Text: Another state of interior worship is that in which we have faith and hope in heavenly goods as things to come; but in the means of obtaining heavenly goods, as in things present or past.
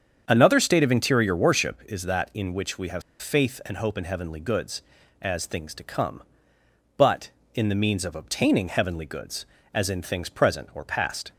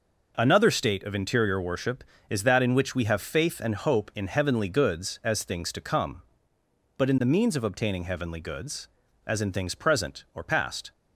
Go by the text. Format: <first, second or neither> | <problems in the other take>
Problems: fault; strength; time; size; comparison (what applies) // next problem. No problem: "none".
second | starts louder than the rest; strong; until 1.2 s; 7.5 dB // pauses between "have" and "faith"; slight; at 3.0 s; 0.18 s long